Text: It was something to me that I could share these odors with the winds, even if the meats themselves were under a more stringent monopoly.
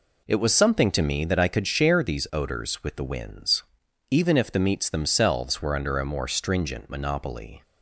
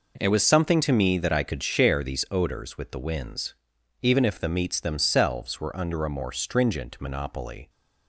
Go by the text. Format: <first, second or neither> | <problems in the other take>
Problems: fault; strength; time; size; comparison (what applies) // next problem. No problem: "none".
neither | none